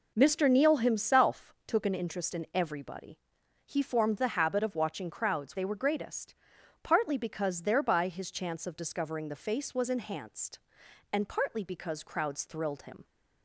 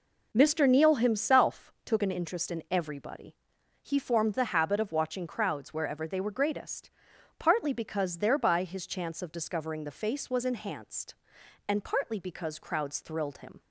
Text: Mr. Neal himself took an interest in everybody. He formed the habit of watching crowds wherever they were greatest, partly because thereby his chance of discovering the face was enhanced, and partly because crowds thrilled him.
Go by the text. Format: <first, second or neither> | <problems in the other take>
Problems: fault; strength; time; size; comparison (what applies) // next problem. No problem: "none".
second | skips "wherever"; at 5.5 s